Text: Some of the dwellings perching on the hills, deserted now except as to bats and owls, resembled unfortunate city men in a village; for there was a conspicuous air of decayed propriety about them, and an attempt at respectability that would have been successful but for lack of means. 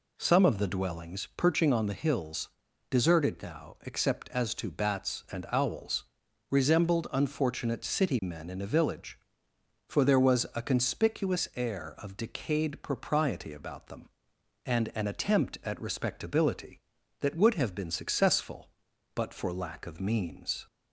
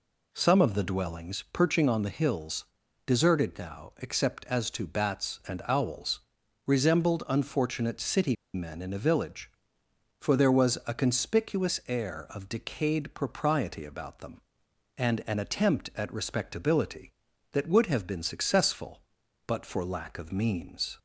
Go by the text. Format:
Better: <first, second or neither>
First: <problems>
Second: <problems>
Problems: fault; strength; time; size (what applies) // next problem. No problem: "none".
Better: first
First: none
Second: pauses between "city" and "men"; slight; at 8.3 s; 0.20 s long